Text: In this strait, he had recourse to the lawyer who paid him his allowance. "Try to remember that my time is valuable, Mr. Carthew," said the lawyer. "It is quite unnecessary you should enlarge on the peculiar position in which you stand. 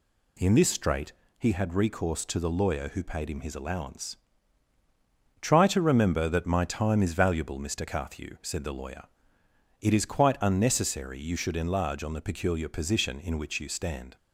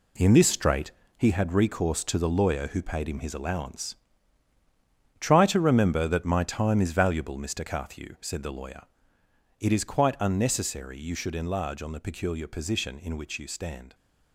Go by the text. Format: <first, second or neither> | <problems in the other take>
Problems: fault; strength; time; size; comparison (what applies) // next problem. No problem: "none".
first | gets quieter; strong; throughout; 9 dB